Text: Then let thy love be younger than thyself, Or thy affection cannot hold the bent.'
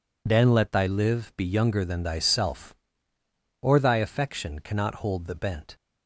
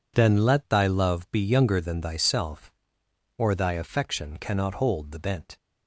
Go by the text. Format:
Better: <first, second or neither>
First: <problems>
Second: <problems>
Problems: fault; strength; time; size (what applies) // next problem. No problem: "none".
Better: second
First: says "live" for "love"; at 0.8 s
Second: none